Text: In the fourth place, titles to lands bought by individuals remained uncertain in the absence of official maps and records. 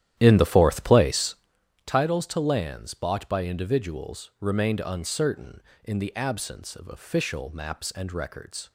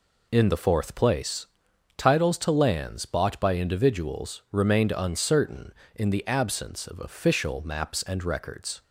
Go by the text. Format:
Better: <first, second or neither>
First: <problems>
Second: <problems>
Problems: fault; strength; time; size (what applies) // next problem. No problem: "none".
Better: second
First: starts louder than the rest; strong; until 1.6 s; 11.5 dB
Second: none